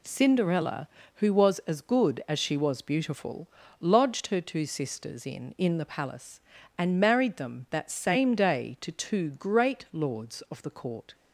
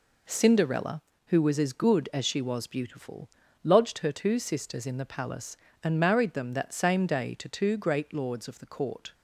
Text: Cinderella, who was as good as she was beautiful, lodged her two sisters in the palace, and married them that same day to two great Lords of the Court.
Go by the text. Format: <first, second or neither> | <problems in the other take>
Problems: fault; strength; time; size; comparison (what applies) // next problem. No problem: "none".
second | says "in" twice; at 5.5 s